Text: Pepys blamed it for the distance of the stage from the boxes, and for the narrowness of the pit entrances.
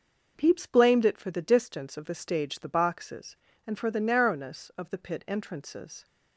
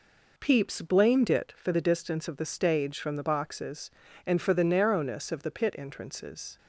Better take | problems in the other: second | skips "from"; at 2.5 s

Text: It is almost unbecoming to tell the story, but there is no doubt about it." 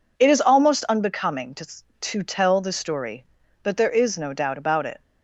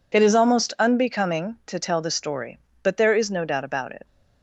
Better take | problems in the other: second | says "to" twice; at 1.9 s

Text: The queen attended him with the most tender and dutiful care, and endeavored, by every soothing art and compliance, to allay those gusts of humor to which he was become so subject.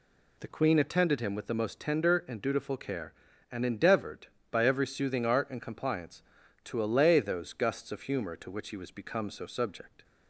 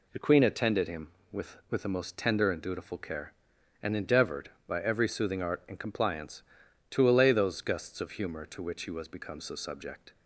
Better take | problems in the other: first | says "with" twice; at 1.6 s

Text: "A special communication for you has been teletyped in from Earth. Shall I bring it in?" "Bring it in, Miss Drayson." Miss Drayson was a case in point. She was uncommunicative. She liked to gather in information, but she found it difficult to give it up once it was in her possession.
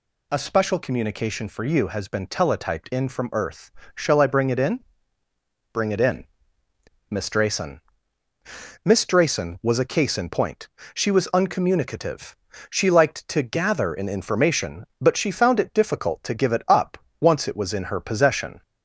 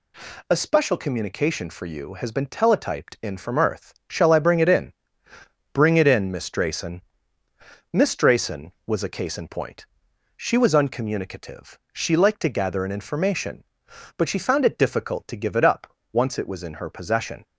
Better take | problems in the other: neither | pauses between "up" and "once"; slight; the same in both

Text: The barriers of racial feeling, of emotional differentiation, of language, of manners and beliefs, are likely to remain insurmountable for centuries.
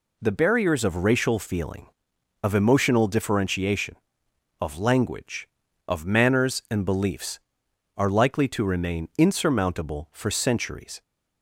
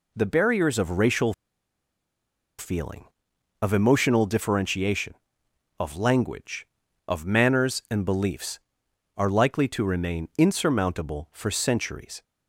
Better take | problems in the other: first | pauses between "racial" and "feeling"; strong; at 1.3 s; 1.2 s long

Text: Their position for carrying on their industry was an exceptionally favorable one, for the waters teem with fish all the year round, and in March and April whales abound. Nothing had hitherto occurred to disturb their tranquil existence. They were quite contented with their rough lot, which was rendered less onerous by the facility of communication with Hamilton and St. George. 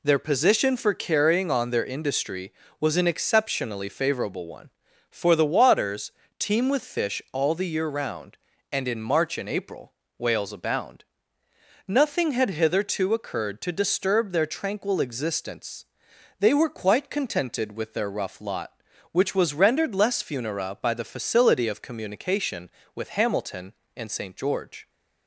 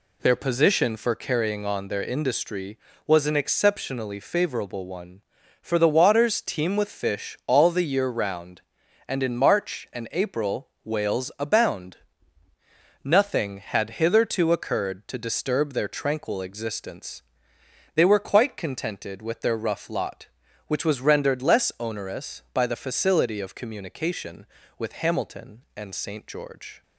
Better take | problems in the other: second | pauses between "waters" and "teem"; slight; at 6.1 s; 0.28 s long // pauses between "April" and "whales"; slight; at 9.9 s; 0.24 s long; slight in the second // says "funera" for "onerous"; at 20.2 s

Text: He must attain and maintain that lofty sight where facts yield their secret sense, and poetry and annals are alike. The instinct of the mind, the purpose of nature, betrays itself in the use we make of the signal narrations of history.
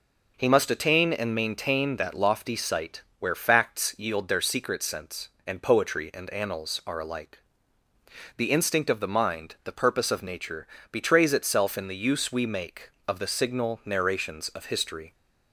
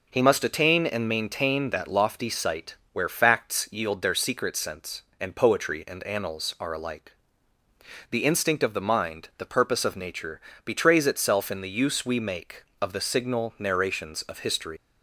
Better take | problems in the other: first | pauses between "sight" and "where"; slight; at 2.7 s; 0.18 s long; slight in the first // leaves "history" unfinished; at 14.7 s; 110 ms

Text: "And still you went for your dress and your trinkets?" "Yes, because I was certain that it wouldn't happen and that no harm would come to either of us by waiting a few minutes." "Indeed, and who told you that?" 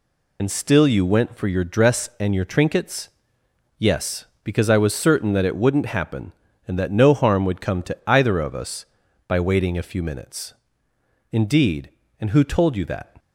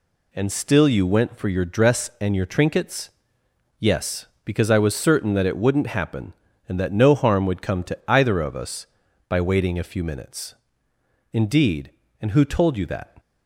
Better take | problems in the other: second | loses the start of "And"; at 0.3 s; 75 ms

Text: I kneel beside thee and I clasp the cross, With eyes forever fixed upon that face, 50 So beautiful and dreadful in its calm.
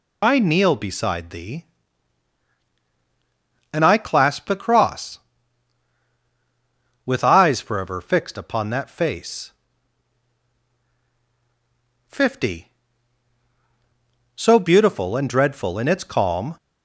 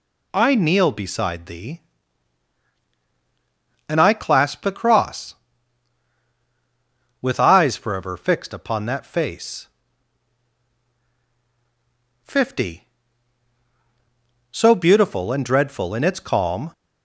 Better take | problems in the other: second | loses the start of "I"; at 0.2 s; 60 ms

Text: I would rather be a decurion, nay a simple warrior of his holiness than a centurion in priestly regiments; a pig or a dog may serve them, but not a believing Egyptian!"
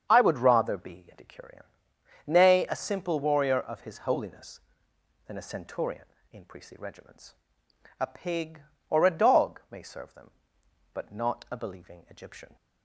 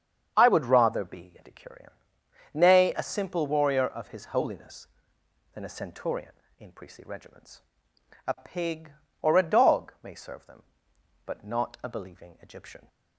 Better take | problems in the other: neither | starts louder than the rest; strong; the same in both

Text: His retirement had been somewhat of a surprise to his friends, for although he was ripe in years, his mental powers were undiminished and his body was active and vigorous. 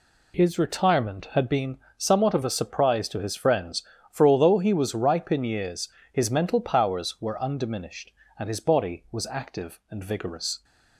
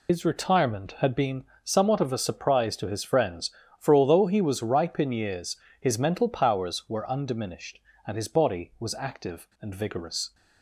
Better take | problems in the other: first | loses the start of "His"; at 0.0 s; 90 ms // pauses between "been" and "somewhat"; slight; at 1.4 s; 0.20 s long; slight in the first

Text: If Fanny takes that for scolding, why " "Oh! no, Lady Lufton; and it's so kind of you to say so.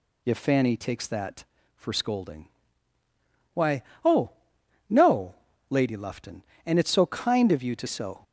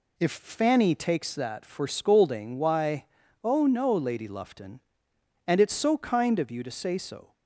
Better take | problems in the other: second | skips "say"; at 7.8 s

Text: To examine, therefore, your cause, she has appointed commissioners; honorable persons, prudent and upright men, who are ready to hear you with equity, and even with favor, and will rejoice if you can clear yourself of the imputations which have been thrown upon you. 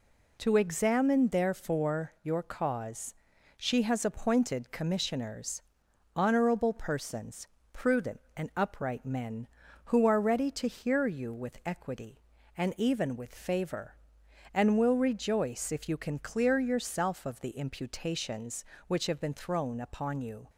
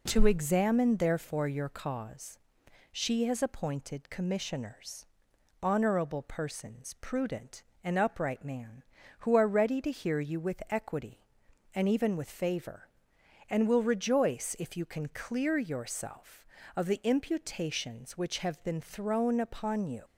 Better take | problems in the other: first | says "man" for "men"; at 8.4 s

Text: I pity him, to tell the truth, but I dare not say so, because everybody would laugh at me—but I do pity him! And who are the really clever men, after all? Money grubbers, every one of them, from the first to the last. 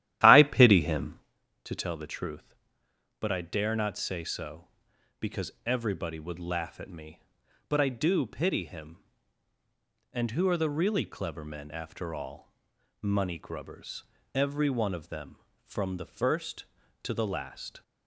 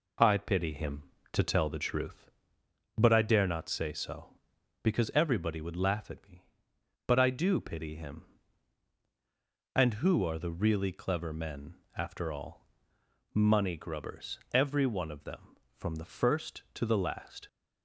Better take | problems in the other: second | starts louder than the rest; strong; until 1.4 s; 13 dB // pauses between "because" and "everybody"; slight; at 5.4 s; 0.16 s long

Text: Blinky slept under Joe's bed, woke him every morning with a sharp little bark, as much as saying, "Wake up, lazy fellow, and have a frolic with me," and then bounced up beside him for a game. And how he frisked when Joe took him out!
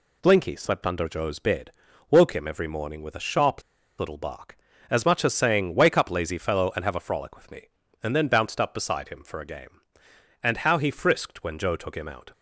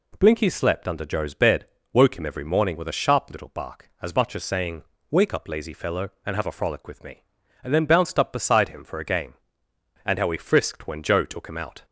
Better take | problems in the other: second | pauses between "sharp" and "little"; at 3.6 s; 0.37 s long

